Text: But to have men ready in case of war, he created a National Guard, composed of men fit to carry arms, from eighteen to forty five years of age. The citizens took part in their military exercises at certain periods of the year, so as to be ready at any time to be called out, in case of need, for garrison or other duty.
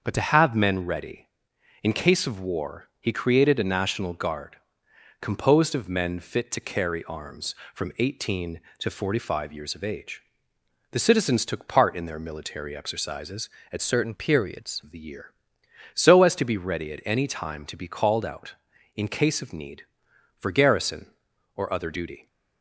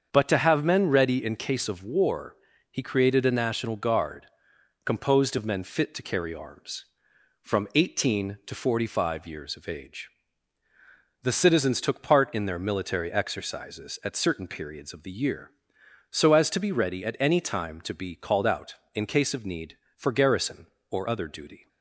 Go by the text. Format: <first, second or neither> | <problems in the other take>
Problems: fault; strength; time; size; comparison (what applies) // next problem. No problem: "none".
second | starts louder than the rest; until 1.0 s; 6.5 dB; strong in the second // changes voice from "certain" to "periods"; from 13.8 to 14.8 s; 1.0 s long